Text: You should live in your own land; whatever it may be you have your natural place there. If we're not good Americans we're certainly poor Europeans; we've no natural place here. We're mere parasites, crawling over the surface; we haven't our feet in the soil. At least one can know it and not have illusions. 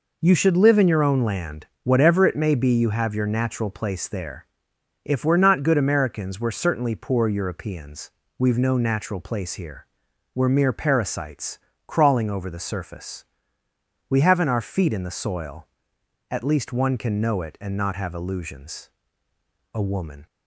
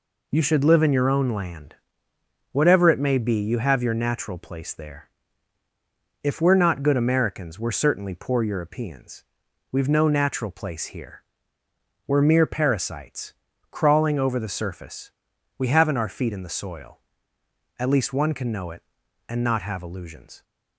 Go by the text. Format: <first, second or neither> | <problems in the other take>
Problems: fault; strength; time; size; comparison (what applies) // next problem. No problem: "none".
second | goes on to say "A woman"; from 19.7 s on; 0.52 s long